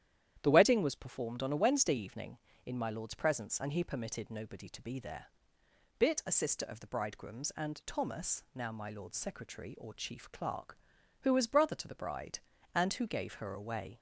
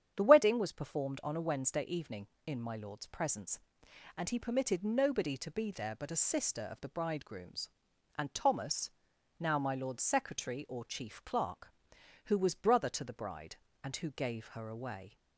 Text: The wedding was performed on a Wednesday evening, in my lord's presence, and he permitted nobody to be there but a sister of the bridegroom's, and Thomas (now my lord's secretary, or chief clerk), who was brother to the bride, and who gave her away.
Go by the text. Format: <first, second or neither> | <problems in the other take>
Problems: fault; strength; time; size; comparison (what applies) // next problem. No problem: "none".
second | starts louder than the rest; strong; until 1.4 s; 10.5 dB; strong in the second // says "bit" for "but"; at 5.9 s